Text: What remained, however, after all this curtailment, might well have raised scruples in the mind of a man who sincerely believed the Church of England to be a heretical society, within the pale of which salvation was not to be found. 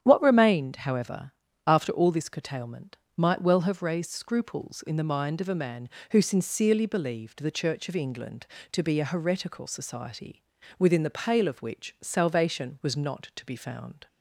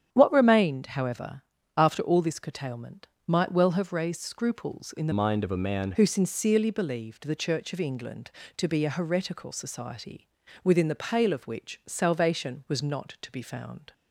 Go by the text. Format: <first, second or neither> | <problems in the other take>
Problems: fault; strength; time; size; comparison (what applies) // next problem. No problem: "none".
first | starts louder than the rest; strong; until 1.1 s; 9 dB; strong in the first // changes voice from "mind" to "man"; from 5.1 to 5.9 s; 0.8 s long